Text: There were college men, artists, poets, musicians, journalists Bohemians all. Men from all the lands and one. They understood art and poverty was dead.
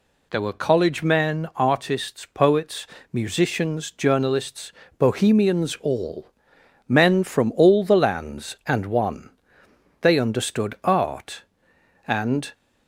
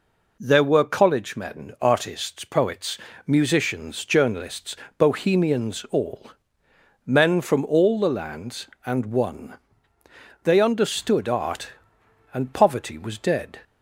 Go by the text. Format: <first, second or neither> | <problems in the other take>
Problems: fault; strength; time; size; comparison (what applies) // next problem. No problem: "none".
second | pauses between "journalists" and "Bohemians"; slight; at 4.7 s; 0.28 s long; slight in the second // stops before "poverty was dead"; at 12.5 s